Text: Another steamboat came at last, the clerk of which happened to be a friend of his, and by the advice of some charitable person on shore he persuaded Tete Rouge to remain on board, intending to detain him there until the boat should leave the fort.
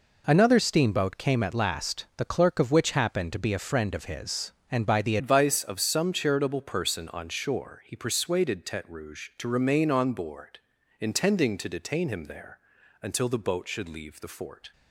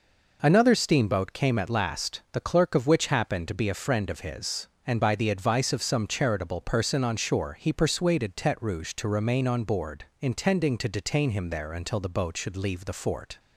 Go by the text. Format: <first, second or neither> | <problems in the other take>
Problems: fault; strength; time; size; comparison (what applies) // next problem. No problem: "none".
second | changes voice at "advice"; from 5.1 s on; 9.6 s long // pauses between "there" and "until"; at 12.5 s; 0.44 s long